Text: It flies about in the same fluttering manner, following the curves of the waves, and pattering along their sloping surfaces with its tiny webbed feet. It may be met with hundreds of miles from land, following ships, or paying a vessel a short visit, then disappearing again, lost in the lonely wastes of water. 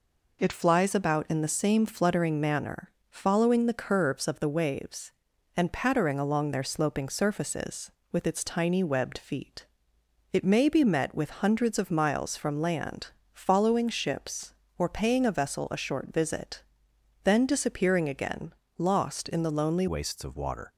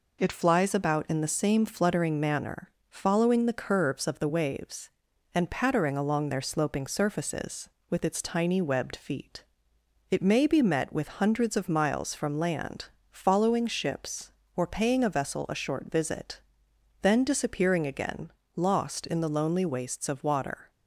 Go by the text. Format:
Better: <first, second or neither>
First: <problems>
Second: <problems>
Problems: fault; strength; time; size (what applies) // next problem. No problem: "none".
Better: second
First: changes voice at "wastes"; from 19.8 s on; 0.9 s long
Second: none